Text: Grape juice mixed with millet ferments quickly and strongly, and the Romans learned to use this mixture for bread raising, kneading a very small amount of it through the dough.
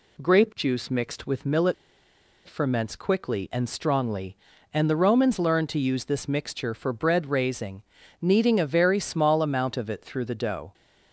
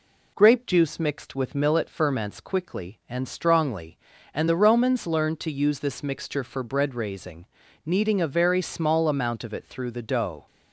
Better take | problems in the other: second | pauses between "millet" and "ferments"; noticeable; at 1.7 s; 0.72 s long

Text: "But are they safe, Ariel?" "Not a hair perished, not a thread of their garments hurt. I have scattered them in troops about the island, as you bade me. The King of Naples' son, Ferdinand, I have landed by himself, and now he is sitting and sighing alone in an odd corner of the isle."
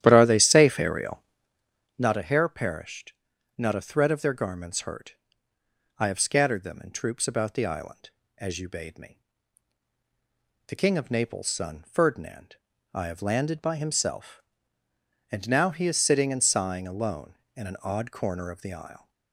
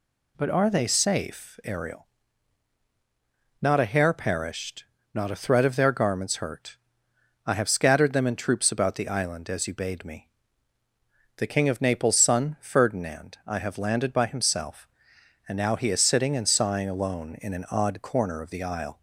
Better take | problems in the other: second | starts louder than the rest; strong; until 1.4 s; 11.5 dB

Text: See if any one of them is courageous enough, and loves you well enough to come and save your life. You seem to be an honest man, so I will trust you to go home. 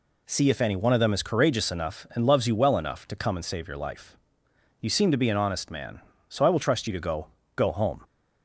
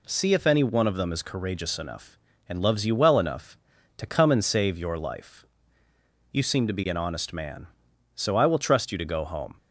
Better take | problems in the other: second | says "go" twice; at 7.5 s

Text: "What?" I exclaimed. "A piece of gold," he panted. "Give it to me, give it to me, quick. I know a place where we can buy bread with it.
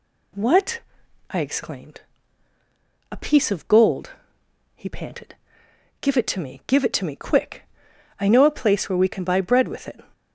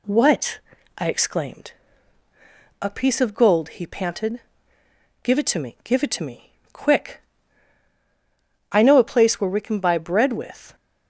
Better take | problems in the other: first | stops before "it"; at 10.7 s

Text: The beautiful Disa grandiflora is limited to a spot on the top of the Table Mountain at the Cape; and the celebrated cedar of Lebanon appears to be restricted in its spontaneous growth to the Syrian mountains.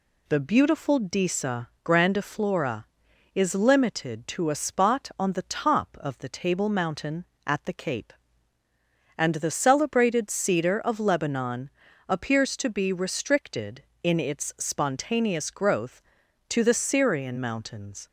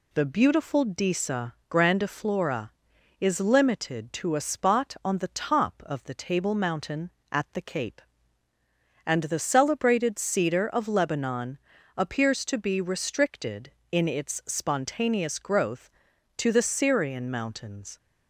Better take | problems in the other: neither | pauses between "Disa" and "grandiflora"; slight; the same in both // pauses between "Lebanon" and "appears"; the same in both

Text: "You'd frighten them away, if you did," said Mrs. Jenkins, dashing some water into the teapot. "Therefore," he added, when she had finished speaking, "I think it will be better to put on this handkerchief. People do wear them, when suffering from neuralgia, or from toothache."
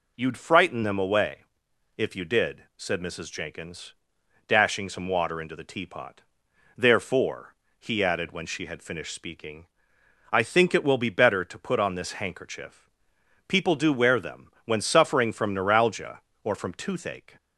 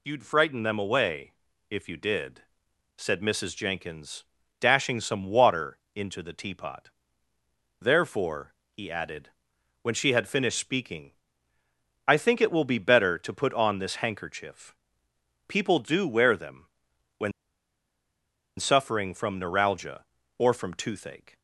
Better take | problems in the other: first | pauses between "water" and "into"; slight; at 5.7 s; 0.16 s long // pauses between "when" and "suffering"; strong; at 17.3 s; 1.2 s long

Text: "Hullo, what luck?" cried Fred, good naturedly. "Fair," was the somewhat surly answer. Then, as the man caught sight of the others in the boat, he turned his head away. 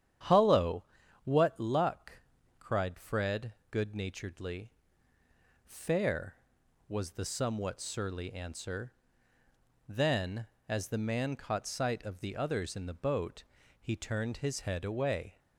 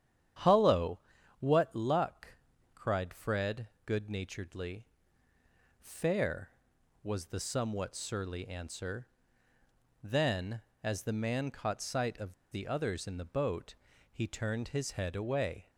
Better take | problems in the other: first | starts louder than the rest; strong; until 1.8 s; 9.5 dB; strong in the first // pauses between "of" and "the"; slight; at 12.3 s; 0.16 s long

